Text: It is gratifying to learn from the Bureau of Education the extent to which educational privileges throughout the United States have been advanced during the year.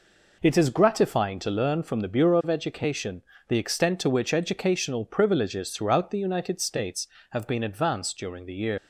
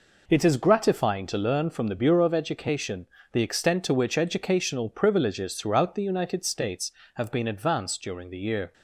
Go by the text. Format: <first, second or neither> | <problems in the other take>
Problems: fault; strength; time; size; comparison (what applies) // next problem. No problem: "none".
second | pauses between "Education" and "the"; slight; at 3.2 s; 0.28 s long; slight in the second // leaves "year" unfinished; at 8.7 s; 105 ms